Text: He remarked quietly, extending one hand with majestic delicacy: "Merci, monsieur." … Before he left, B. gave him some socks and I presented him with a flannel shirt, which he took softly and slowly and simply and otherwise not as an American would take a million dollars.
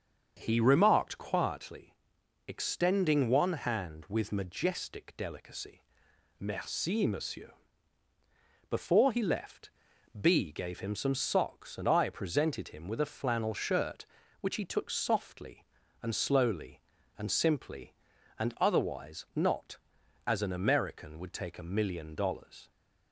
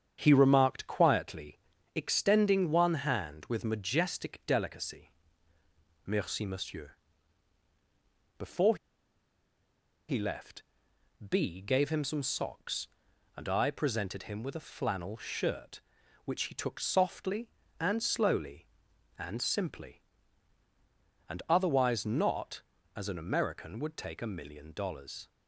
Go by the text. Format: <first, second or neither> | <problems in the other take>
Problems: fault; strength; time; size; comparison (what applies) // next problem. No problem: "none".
first | starts louder than the rest; strong; until 1.2 s; 8 dB; also in the first // pauses between "Before" and "he"; strong; at 8.7 s; 1.3 s long